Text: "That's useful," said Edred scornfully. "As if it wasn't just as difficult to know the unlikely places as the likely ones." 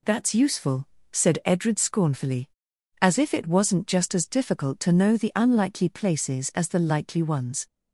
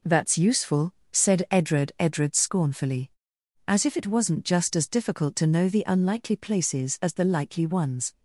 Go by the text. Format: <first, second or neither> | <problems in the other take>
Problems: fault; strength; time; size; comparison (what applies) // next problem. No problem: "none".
first | says "Edred" twice; at 1.9 s